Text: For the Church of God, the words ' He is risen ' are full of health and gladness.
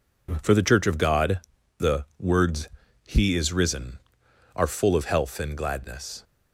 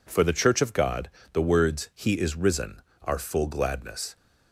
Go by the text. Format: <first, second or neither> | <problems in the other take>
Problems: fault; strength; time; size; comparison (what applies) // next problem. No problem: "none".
first | skips "of health and"; at 3.4 s